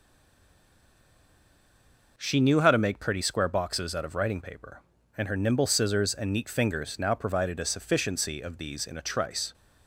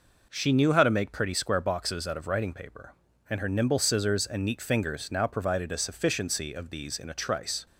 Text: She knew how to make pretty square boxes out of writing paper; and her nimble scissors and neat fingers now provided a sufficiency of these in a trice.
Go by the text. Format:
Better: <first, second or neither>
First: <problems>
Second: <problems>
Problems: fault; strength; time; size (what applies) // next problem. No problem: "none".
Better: second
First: stays silent before the first word; until 2.1 s; 2.1 s long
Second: none